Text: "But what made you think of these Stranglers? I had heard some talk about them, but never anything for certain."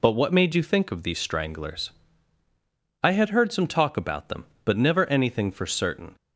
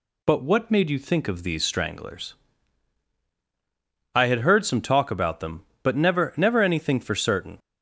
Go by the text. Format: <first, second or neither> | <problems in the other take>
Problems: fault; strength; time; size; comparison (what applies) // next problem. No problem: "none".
first | says "never" twice; at 6.3 s